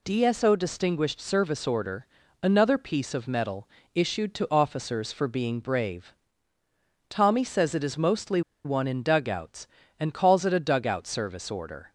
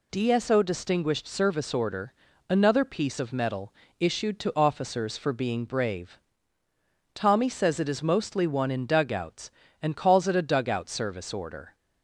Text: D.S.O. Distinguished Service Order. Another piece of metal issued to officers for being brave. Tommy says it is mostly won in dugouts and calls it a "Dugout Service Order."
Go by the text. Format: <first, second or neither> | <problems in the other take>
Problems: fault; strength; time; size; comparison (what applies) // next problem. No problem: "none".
second | pauses between "metal" and "issued"; slight; at 3.6 s; 0.26 s long; slight in the second // pauses between "mostly" and "won"; slight; at 8.4 s; 0.24 s long